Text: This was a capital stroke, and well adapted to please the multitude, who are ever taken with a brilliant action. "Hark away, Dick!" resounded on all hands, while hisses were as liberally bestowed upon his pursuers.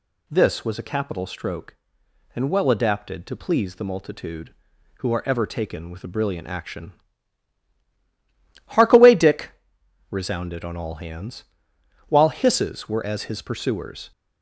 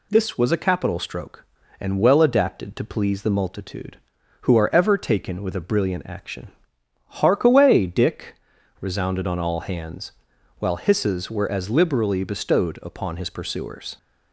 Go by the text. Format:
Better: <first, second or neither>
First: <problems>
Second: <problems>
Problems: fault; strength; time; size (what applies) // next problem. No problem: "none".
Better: second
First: skips "liberally bestowed upon"; at 13.2 s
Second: none